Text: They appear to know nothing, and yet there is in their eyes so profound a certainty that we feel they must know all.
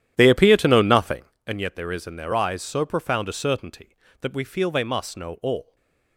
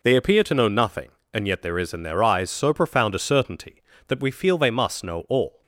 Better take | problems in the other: second | starts louder than the rest; strong; until 1.5 s; 11 dB // stays silent after the last word; slight; from 5.6 s on; 0.5 s long

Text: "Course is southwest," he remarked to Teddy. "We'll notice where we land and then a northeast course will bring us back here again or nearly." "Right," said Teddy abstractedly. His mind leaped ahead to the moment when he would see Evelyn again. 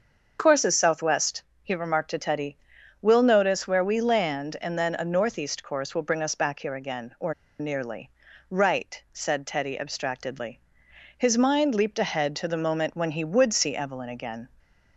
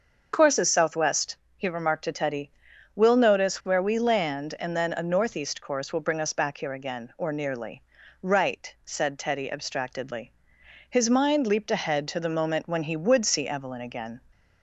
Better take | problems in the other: second | starts louder than the rest; until 1.4 s; 6.5 dB; also in the second // pauses between "or" and "nearly"; slight; at 7.3 s; 0.26 s long

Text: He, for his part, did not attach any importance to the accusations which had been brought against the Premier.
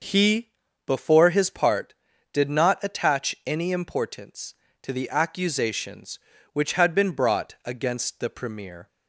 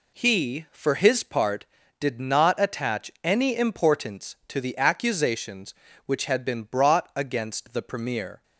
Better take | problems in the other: second | says "before" for "for"; at 0.8 s

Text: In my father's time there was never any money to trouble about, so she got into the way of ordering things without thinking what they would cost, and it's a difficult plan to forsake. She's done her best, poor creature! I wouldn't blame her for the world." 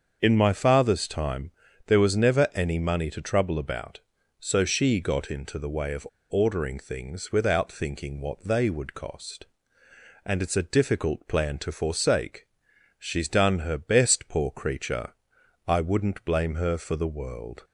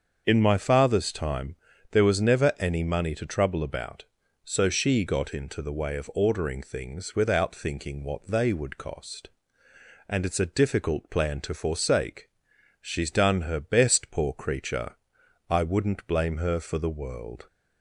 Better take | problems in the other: second | starts louder than the rest; until 1.2 s; 6.5 dB; also in the second // pauses between "time" and "there"; at 1.4 s; 0.38 s long; also in the second // pauses between "of" and "ordering"; slight; at 6.0 s; 0.22 s long

